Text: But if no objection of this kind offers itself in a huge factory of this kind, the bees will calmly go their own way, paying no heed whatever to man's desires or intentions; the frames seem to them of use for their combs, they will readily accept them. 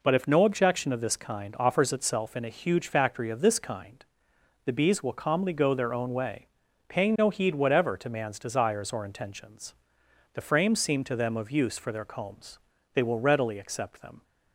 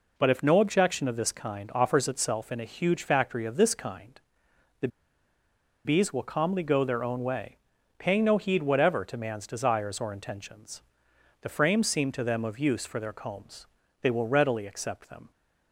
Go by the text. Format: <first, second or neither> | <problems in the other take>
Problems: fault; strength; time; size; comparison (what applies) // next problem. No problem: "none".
first | pauses between "the" and "bees"; noticeable; at 4.8 s; 0.96 s long